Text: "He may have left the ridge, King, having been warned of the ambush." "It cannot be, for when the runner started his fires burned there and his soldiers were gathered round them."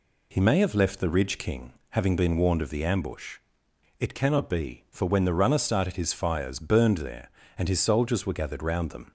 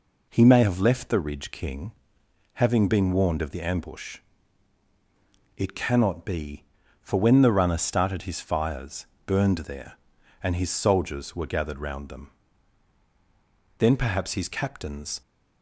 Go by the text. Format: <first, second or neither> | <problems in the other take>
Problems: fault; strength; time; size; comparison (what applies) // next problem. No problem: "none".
first | pauses between "fires" and "burned"; slight; at 9.0 s; 0.18 s long // goes on to say "Then perhaps his captains"; from 13.7 s on; 1.4 s long